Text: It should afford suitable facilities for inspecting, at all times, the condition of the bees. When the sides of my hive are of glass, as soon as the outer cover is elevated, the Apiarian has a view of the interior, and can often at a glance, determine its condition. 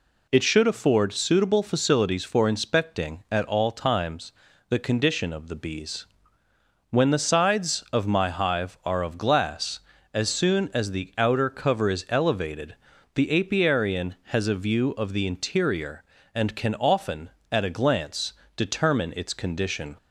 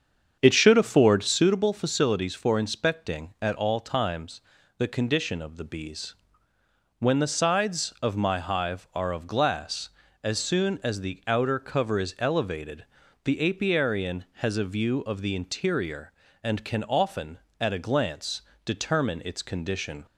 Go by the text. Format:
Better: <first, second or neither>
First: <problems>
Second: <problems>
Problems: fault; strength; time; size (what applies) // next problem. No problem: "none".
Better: first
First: none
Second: starts louder than the rest; strong; until 1.6 s; 7.5 dB